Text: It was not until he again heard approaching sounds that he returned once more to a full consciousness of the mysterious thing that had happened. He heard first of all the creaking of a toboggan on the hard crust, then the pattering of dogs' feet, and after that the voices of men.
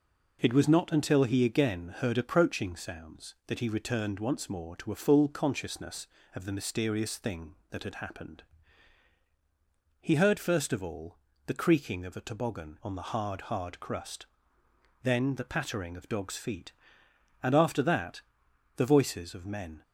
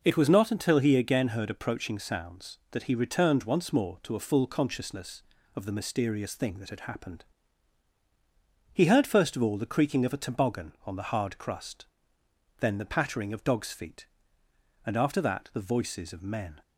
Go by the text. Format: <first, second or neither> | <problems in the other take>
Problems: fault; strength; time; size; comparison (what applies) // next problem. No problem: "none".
second | pauses between "all" and "the"; slight; at 11.1 s; 0.28 s long // says "hard" twice; at 13.4 s // pauses between "that" and "the"; noticeable; at 18.2 s; 0.56 s long